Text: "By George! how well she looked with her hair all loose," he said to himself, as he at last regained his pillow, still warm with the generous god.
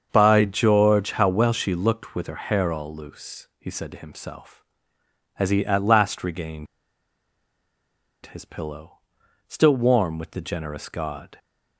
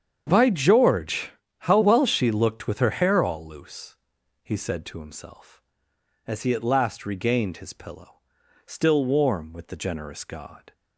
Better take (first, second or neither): second